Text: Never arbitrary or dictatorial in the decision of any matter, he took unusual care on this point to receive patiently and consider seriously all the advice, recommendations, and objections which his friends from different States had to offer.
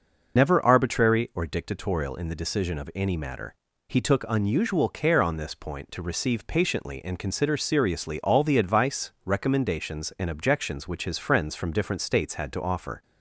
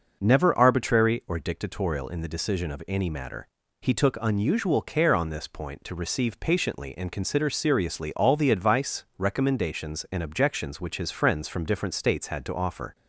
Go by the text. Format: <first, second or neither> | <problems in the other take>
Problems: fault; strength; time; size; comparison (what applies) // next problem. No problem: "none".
second | loses the start of "Never"; at 0.3 s; 80 ms